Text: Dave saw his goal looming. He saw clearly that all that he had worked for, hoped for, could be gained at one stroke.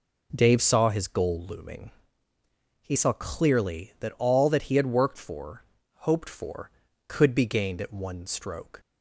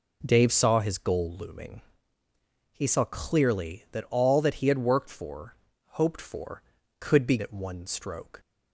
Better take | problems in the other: first | skips "gained"; at 7.3 s

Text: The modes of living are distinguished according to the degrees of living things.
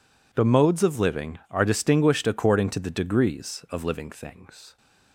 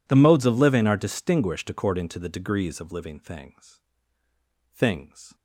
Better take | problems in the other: first | says "things" twice; at 4.7 s

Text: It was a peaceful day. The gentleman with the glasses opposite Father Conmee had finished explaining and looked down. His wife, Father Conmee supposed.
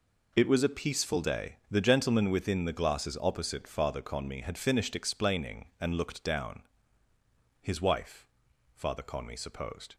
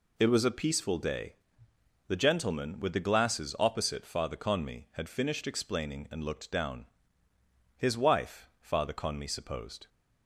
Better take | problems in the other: second | says "within" for "with"; at 2.3 s

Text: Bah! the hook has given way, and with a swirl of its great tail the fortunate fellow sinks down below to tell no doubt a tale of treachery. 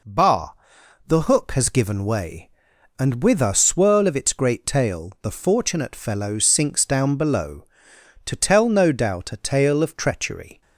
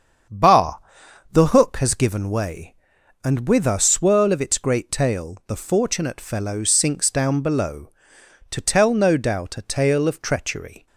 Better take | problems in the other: first | starts louder than the rest; strong; until 1.8 s; 7.5 dB

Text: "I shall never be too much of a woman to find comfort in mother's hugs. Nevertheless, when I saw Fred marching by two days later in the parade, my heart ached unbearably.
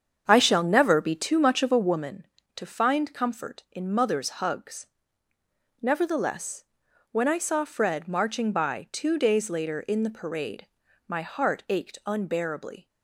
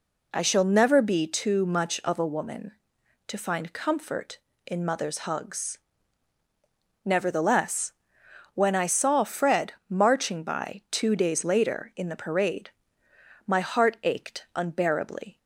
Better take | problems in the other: second | starts louder than the rest; strong; until 2.1 s; 7.5 dB

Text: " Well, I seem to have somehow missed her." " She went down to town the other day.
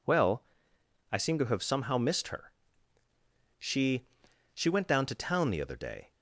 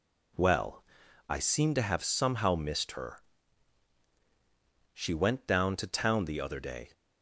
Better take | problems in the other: second | says "She" twice; at 4.5 s

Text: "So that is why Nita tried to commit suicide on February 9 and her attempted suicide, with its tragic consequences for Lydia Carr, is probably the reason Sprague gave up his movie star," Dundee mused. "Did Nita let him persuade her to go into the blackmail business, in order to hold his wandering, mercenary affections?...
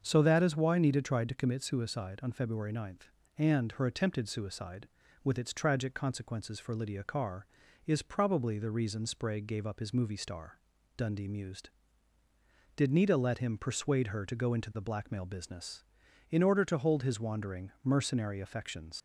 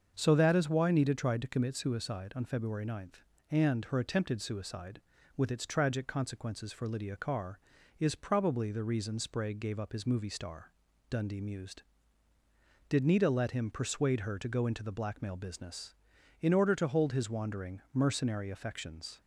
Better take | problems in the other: second | starts louder than the rest; until 1.0 s; 6.5 dB; also in the second // leaves "affections" unfinished; at 18.9 s; 100 ms

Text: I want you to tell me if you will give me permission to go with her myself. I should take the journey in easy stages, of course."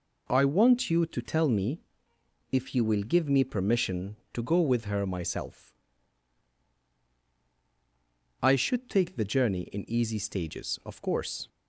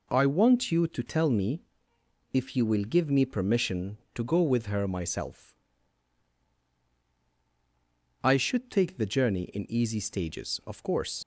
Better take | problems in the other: first | pauses between "me" and "if"; noticeable; at 1.6 s; 0.70 s long; noticeable in the first // leaves "course" unfinished; at 11.2 s; 70 ms

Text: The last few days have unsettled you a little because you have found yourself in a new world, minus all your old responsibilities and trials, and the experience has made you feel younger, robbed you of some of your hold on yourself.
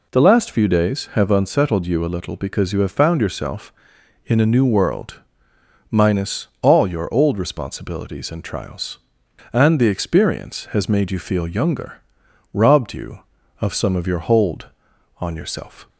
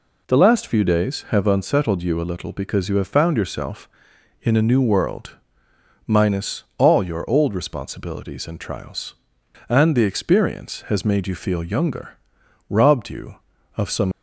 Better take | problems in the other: first | pauses between "minus" and "all"; slight; at 6.6 s; 0.16 s long; slight in the first // stops before "of your hold on yourself"; at 14.1 s

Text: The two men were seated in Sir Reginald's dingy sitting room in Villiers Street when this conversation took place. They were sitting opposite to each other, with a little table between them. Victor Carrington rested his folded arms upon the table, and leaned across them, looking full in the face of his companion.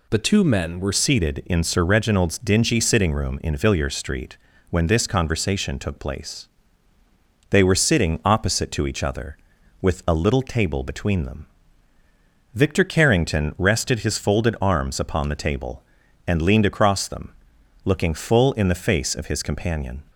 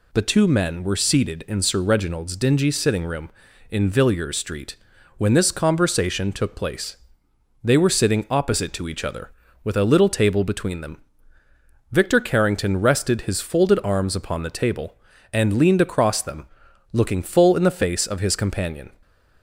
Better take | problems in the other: second | changes voice at "seated"; from 0.9 s on; 19.1 s long // pauses between "Street" and "when"; slight; at 4.3 s; 0.32 s long; also in the second

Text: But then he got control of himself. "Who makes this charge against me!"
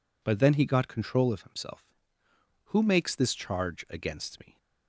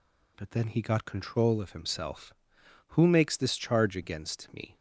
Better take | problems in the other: neither | none

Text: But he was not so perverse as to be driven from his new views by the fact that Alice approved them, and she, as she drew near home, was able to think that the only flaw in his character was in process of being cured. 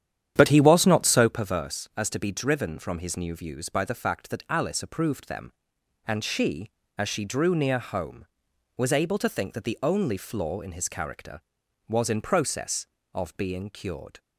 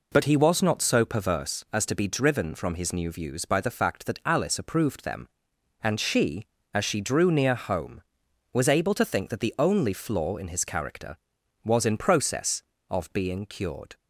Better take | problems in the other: second | starts louder than the rest; strong; until 1.4 s; 10 dB

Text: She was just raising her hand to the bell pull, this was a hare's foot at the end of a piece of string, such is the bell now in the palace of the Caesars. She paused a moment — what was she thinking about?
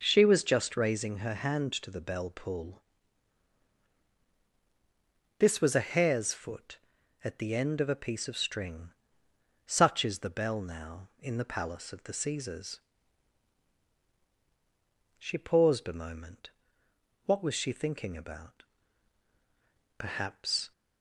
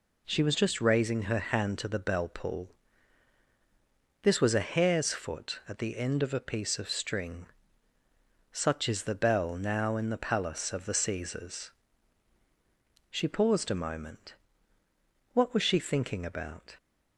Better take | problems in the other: second | goes on to say "Perhaps"; noticeable; from 19.9 s on; 0.72 s long

